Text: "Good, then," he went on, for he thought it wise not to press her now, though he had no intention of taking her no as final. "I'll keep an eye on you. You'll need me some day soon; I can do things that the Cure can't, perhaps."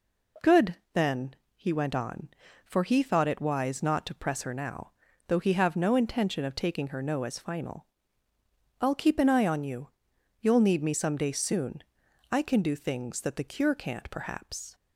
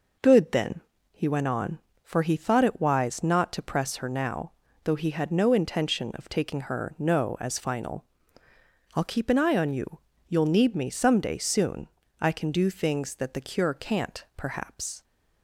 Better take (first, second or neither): second